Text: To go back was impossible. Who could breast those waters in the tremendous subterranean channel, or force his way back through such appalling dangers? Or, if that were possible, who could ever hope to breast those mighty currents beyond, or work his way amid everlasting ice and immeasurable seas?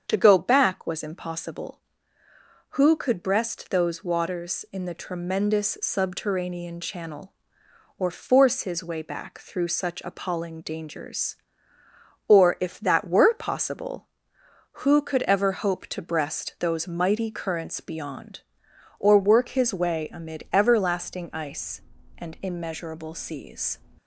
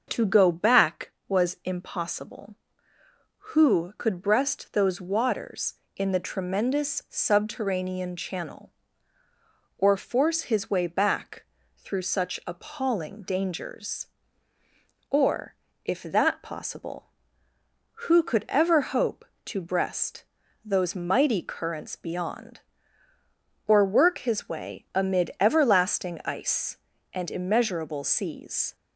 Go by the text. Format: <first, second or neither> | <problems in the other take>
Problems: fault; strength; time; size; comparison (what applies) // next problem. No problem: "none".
first | starts louder than the rest; until 1.0 s; 6.5 dB; strong in the first // pauses between "back" and "through"; slight; at 11.4 s; 0.32 s long // skips "were"; at 16.4 s // pauses between "breast" and "those"; at 20.2 s; 0.42 s long